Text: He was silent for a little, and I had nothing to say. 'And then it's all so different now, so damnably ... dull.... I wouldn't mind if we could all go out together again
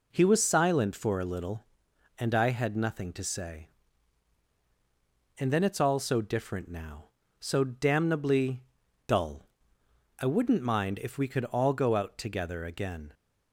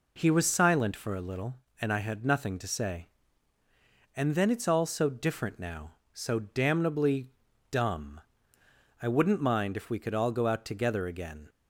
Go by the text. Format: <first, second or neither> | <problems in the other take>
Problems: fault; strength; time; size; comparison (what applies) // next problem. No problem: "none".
first | says "dumb" for "dull"; at 7.6 s